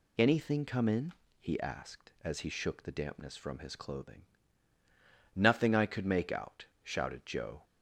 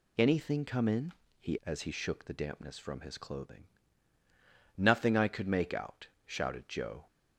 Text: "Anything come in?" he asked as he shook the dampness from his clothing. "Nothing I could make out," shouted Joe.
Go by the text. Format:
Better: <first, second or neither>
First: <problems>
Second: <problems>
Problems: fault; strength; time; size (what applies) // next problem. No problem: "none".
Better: first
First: none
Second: skips "asked"; at 1.6 s